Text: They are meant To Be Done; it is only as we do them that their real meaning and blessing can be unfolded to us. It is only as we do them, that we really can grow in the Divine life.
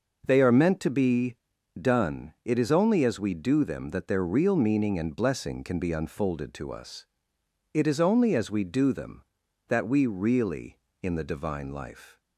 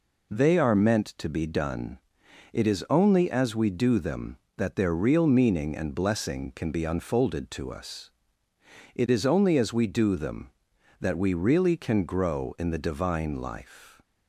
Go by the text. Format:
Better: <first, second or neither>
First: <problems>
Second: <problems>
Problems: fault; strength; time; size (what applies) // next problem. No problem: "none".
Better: second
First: pauses between "Be" and "Done"; at 1.3 s; 0.44 s long // skips "can grow"; at 10.8 s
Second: none